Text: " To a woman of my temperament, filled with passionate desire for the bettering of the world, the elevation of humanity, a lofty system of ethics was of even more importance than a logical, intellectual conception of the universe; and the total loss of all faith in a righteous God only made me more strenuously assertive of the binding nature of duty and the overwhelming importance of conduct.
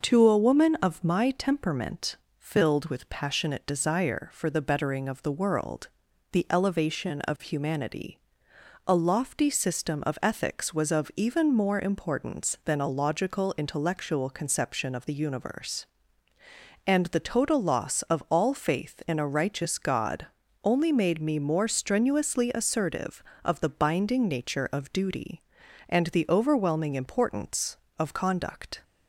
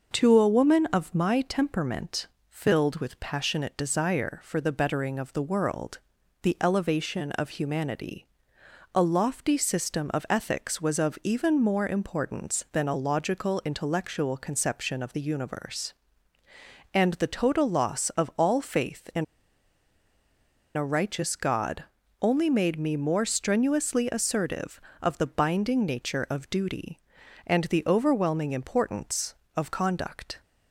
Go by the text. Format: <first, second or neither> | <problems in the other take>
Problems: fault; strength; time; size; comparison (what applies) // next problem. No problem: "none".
first | pauses between "in" and "a"; strong; at 19.2 s; 1.5 s long // pauses between "God" and "only"; slight; at 21.8 s; 0.36 s long; slight in the first